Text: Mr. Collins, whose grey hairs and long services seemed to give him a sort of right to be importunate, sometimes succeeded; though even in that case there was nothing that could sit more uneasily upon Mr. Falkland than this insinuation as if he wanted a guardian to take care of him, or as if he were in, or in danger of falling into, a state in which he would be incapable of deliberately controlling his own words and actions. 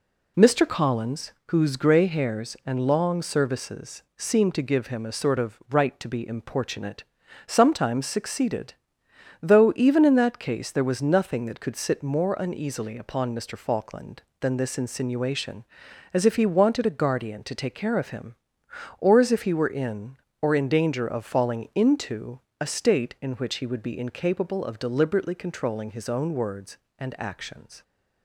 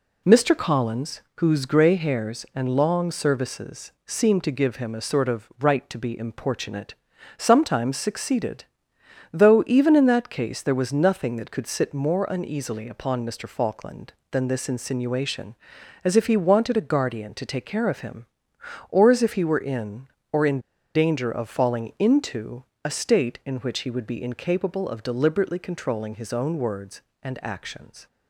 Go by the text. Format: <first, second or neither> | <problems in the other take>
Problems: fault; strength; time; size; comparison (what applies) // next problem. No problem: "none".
first | pauses between "in" and "danger"; slight; at 20.5 s; 0.35 s long